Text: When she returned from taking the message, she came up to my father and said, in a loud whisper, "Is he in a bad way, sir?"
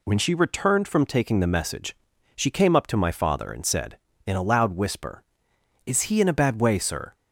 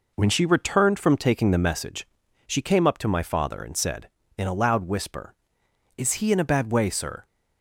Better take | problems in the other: first | starts louder than the rest; noticeable; until 1.8 s; 4.5 dB

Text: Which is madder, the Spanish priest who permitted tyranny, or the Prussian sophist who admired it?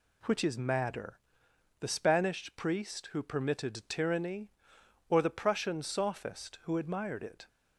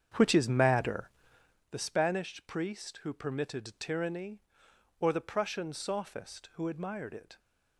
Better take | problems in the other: first | starts louder than the rest; strong; until 1.6 s; 8 dB

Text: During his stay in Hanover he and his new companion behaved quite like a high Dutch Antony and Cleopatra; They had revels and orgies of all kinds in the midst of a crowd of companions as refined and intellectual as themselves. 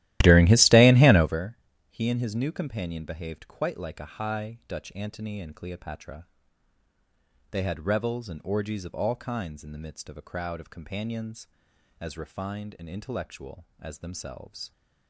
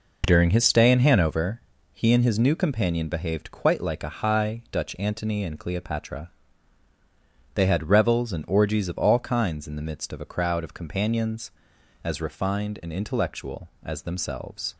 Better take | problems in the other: second | starts louder than the rest; strong; until 1.5 s; 15 dB // pauses between "Hanover" and "he"; slight; at 1.5 s; 0.32 s long; slight in the second

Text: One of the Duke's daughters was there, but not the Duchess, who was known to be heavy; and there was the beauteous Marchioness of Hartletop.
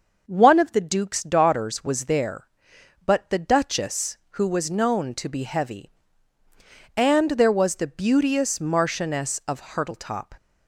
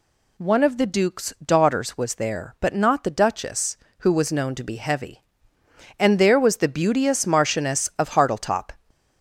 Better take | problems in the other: second | starts louder than the rest; noticeable; until 1.2 s; 6 dB // skips "not"; at 3.2 s

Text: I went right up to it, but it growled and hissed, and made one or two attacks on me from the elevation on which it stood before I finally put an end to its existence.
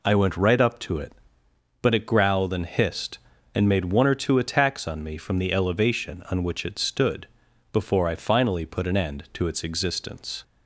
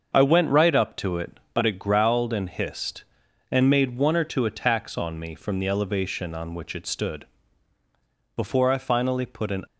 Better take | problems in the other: first | starts louder than the rest; until 1.1 s; 6.5 dB // pauses between "stood" and "before"; at 7.2 s; 1.0 s long; also in the first // stops before "end to its existence"; at 9.6 s

